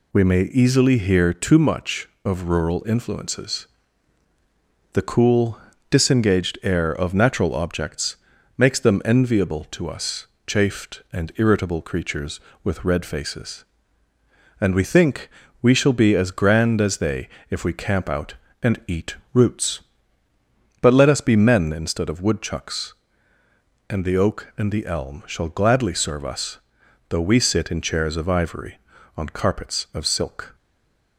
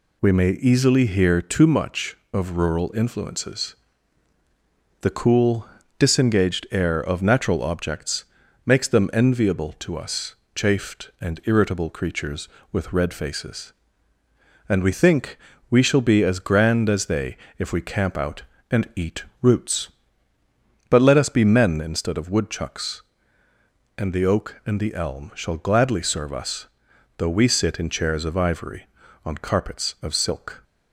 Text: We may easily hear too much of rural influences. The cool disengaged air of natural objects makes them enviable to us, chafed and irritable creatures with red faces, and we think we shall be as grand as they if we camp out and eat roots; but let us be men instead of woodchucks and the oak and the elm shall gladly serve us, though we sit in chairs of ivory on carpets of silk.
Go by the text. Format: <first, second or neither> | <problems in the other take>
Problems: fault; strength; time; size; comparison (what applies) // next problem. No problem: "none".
second | pauses between "cool" and "disengaged"; slight; at 5.5 s; 0.32 s long; slight in the second // pauses between "objects" and "makes"; at 8.1 s; 0.40 s long; also in the second // pauses between "think" and "we"; slight; at 15.2 s; 0.32 s long; slight in the second // pauses between "they" and "if"; slight; at 17.2 s; 0.20 s long; slight in the second // pauses between "eat" and "roots"; slight; at 19.1 s; 0.18 s long; slight in the second // stays silent after the last word; slight; from 30.5 s on; 0.6 s long